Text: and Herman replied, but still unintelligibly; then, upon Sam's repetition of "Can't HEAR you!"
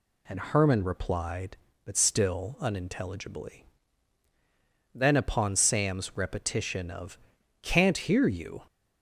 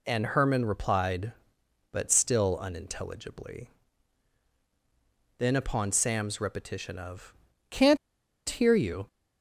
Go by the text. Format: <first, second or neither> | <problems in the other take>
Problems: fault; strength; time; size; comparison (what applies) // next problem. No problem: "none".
first | pauses between "of" and "Can't"; at 7.3 s; 0.38 s long; also in the first // pauses between "Can't" and "HEAR"; noticeable; at 7.9 s; 0.53 s long